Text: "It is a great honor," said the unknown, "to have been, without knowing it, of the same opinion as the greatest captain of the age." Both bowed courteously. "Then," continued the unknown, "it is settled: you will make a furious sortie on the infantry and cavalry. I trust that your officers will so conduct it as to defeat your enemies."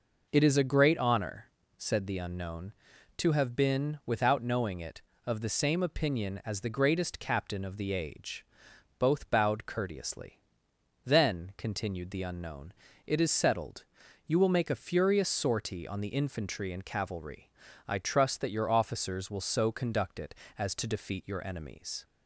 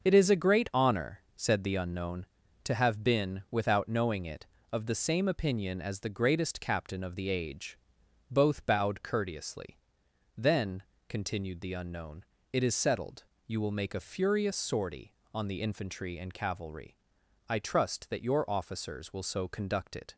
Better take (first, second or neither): first